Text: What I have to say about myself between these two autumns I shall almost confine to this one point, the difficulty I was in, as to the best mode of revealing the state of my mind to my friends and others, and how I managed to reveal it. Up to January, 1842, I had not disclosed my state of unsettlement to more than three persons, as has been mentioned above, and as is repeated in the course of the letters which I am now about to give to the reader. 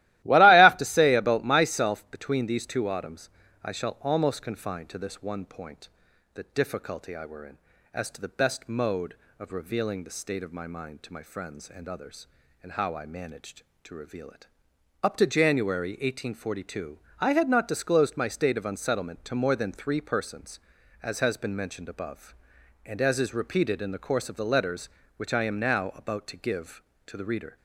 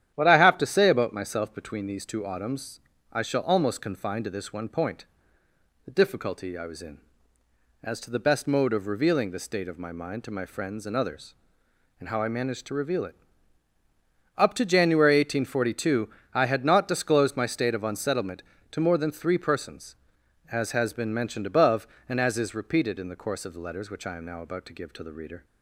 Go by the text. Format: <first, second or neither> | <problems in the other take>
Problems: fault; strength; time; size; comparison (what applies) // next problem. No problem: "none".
second | starts louder than the rest; strong; until 1.2 s; 16 dB; strong in the second // pauses between "autumns" and "I"; slight; at 3.2 s; 0.36 s long; slight in the second // says "were" for "was"; at 7.2 s